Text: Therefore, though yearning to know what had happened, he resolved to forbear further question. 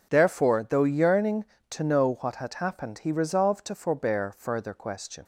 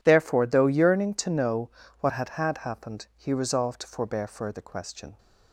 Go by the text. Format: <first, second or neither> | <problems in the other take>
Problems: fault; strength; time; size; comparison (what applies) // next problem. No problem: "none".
first | pauses between "know" and "what"; slight; at 1.6 s; 0.30 s long // says "had" twice; at 2.2 s